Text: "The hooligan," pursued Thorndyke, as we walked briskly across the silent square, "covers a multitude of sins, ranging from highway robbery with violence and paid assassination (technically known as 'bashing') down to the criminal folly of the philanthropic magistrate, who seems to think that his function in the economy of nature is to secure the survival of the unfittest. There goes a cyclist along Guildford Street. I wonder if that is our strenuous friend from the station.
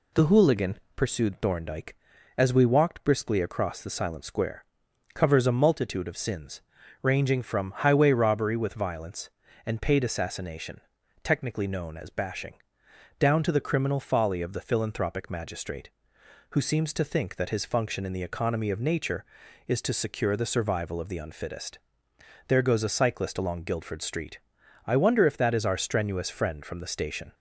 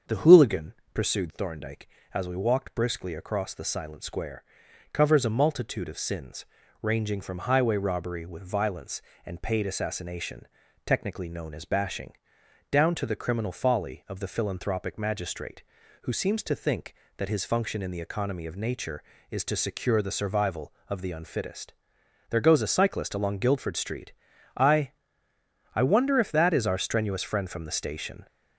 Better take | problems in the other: first | starts louder than the rest; until 1.2 s; 7 dB // says "I" twice; at 25.7 s

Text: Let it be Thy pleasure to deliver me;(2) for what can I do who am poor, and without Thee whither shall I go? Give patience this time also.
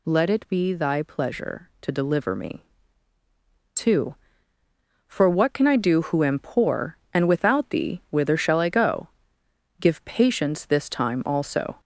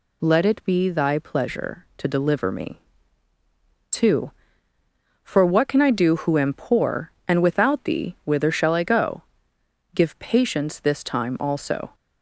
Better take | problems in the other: second | gets louder; strong; throughout; 14.5 dB

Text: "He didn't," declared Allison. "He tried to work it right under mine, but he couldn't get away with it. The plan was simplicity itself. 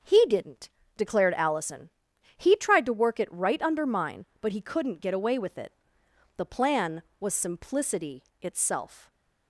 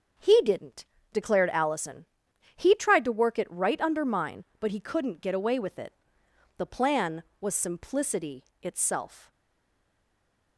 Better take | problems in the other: first | starts louder than the rest; until 1.4 s; 6.5 dB; also in the first // pauses between "simplicity" and "itself"; slight; at 8.4 s; 0.16 s long; slight in the first // stays silent after the last word; noticeable; from 9.3 s on; 1.2 s long

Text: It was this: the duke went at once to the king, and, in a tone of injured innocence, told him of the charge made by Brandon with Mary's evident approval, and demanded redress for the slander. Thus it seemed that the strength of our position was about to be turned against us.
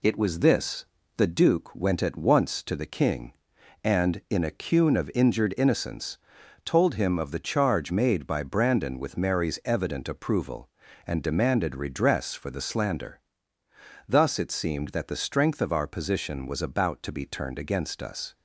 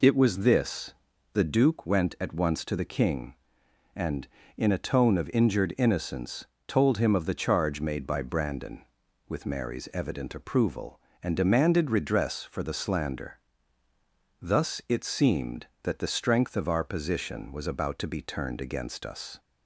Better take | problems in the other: second | says "cune" for "tone"; at 4.5 s

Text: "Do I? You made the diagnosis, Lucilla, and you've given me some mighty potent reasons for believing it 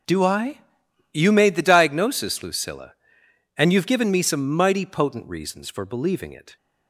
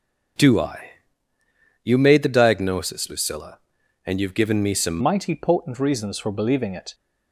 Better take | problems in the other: first | changes voice at "mighty"; from 5.0 s on; 1.9 s long

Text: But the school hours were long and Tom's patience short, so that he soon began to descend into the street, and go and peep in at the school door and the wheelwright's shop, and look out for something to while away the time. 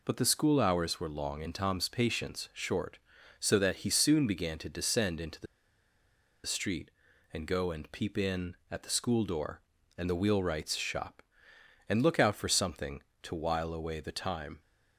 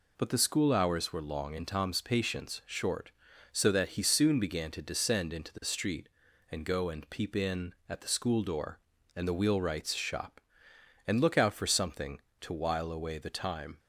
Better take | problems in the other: second | pauses between "the" and "street"; at 5.4 s; 1.0 s long

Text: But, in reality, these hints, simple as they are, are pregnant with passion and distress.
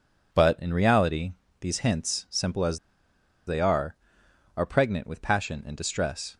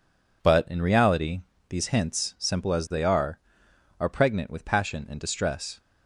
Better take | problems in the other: second | pauses between "as" and "they"; noticeable; at 2.7 s; 0.69 s long

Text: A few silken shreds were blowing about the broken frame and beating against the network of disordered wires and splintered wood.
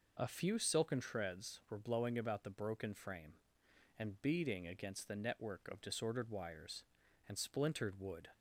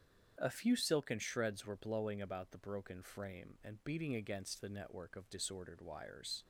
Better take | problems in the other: first | starts louder than the rest; strong; until 1.3 s; 8 dB // stops before "and splintered wood"; at 6.4 s

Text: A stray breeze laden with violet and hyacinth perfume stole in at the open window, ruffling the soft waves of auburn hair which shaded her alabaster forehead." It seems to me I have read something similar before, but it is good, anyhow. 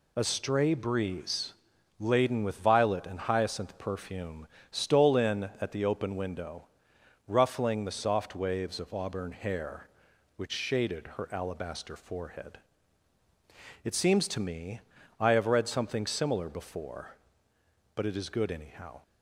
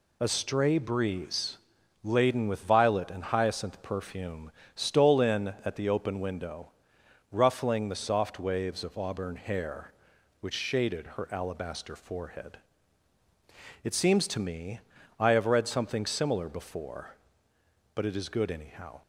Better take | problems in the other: neither | pauses between "breeze" and "laden"; noticeable; the same in both // pauses between "perfume" and "stole"; slight; the same in both // pauses between "me" and "I"; the same in both

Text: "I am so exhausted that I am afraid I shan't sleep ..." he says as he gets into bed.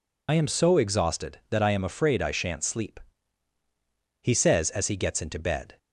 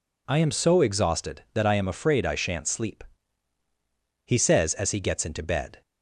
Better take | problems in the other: second | loses the start of "I"; at 0.2 s; 50 ms

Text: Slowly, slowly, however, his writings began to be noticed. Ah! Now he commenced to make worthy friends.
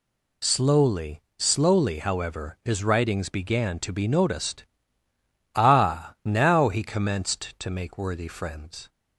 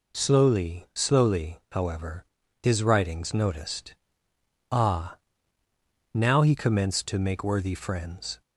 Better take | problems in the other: first | skips "began to be"; at 3.3 s

